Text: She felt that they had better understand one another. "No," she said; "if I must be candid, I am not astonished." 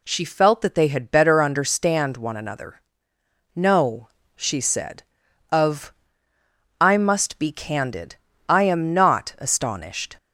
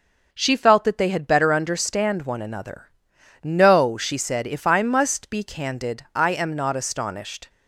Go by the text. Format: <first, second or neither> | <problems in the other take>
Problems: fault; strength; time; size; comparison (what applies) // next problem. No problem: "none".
second | says "of" for "if"; at 5.4 s